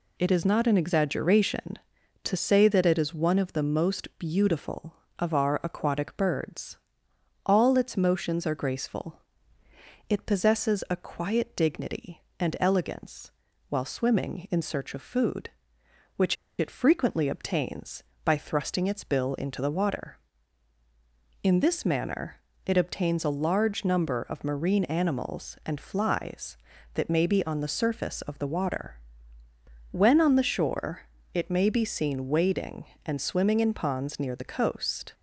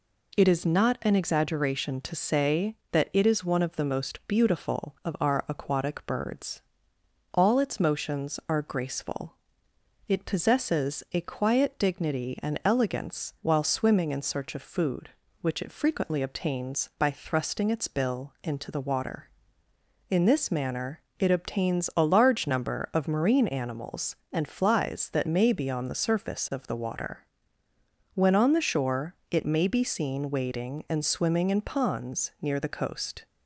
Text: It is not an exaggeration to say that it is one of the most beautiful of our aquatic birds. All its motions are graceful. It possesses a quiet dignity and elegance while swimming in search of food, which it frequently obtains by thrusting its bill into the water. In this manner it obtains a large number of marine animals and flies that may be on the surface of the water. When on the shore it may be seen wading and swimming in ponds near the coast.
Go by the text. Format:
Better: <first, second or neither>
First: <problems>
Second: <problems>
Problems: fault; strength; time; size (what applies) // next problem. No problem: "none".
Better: second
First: pauses between "elegance" and "while"; at 13.3 s; 0.38 s long // pauses between "which" and "it"; slight; at 16.3 s; 0.23 s long // pauses between "manner" and "it"; slight; at 22.3 s; 0.26 s long // pauses between "shore" and "it"; slight; at 31.0 s; 0.30 s long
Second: pauses between "manner" and "it"; slight; at 20.9 s; 0.20 s long // pauses between "shore" and "it"; slight; at 29.1 s; 0.16 s long